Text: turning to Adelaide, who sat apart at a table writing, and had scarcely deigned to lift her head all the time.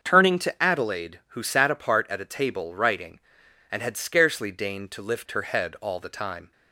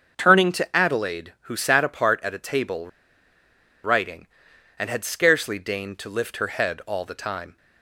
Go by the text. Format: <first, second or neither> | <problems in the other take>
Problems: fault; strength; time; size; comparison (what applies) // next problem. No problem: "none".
first | starts louder than the rest; until 1.1 s; 6.5 dB; also in the first // pauses between "table" and "writing"; noticeable; at 2.8 s; 0.95 s long